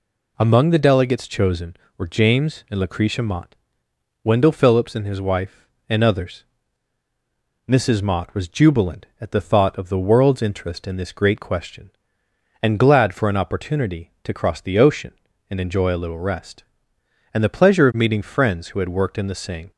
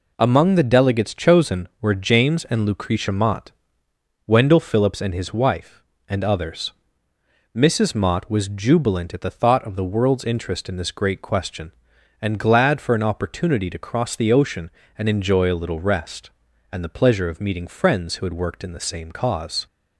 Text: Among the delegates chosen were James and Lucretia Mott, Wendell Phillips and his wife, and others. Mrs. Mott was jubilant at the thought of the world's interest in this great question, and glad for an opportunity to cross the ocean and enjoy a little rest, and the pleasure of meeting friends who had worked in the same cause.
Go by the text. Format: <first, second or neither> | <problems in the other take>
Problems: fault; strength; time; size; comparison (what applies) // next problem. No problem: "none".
second | stops before "cause"; at 19.7 s